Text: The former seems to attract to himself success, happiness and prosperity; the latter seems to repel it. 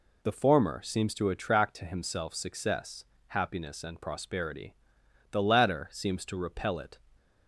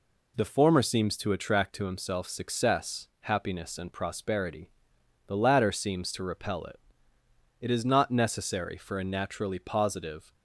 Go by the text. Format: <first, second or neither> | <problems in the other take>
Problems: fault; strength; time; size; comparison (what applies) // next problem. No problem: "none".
first | goes on to say "It is not necessary for a naturally positive"; strong; from 7.6 s on; 2.7 s long